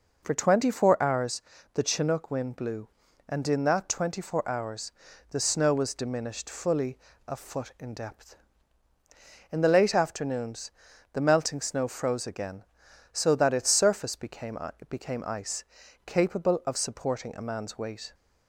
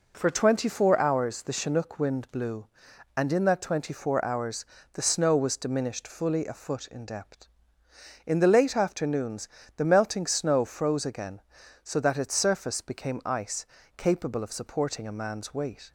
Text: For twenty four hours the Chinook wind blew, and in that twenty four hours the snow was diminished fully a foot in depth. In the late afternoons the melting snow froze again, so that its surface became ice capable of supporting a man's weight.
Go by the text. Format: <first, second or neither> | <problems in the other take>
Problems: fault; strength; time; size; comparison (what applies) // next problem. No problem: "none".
second | pauses between "hours" and "the"; slight; at 1.4 s; 0.32 s long // pauses between "hours" and "the"; at 4.8 s; 0.42 s long; slight in the second // pauses between "fully" and "a"; slight; at 6.9 s; 0.32 s long // pauses between "afternoons" and "the"; at 10.7 s; 0.40 s long; slight in the second // says "became" twice; at 14.8 s // pauses between "ice" and "capable"; at 15.6 s; 0.40 s long; slight in the second